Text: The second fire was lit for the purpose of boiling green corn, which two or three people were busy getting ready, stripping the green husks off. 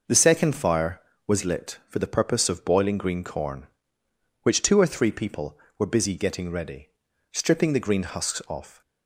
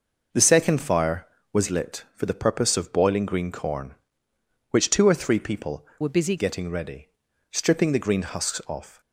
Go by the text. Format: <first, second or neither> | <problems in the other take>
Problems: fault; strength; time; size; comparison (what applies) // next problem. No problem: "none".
first | changes voice from "were" to "busy"; from 6.0 to 6.3 s; 0.3 s long